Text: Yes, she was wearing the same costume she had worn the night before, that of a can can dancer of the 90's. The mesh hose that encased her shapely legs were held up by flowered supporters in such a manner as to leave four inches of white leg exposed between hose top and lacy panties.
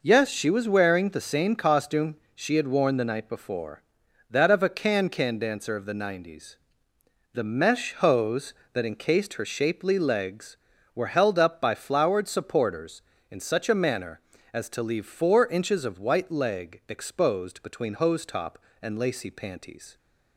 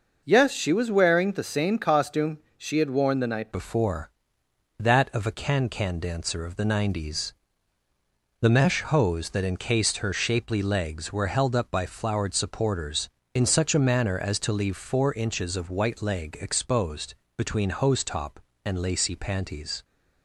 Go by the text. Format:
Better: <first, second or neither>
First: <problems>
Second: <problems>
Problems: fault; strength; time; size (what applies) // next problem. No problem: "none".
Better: first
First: pauses between "costume" and "she"; slight; at 2.1 s; 0.20 s long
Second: pauses between "costume" and "she"; slight; at 2.3 s; 0.20 s long // changes voice at "before"; from 3.5 s on; 16.3 s long // pauses between "exposed" and "between"; slight; at 17.1 s; 0.22 s long